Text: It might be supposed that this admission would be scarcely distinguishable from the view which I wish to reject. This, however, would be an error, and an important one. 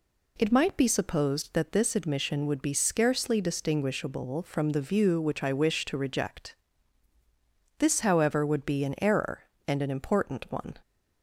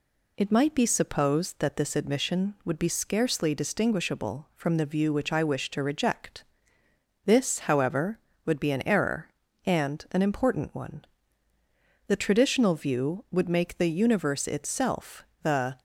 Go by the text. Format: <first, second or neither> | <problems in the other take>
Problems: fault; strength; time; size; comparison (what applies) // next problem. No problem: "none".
first | goes on to say "The traditional view would make the universe itself the"; strong; from 12.0 s on; 3.7 s long